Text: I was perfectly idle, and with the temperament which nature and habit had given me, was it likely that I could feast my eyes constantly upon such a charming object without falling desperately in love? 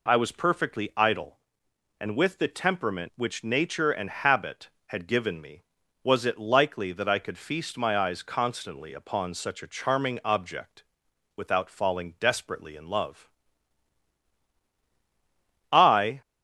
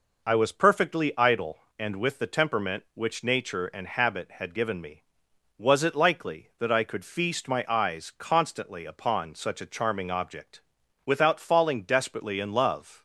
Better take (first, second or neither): second